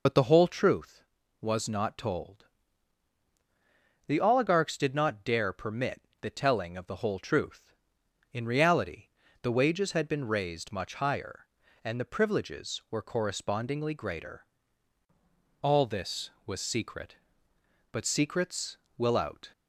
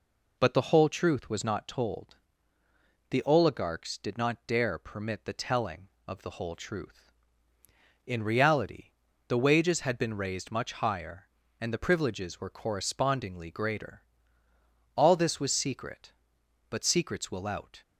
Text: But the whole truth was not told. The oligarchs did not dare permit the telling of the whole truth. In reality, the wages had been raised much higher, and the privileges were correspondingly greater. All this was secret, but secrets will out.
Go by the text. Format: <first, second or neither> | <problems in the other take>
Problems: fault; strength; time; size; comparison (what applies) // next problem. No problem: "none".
second | loses the start of "But"; at 0.0 s; 55 ms // pauses between "permit" and "the"; slight; at 6.0 s; 0.20 s long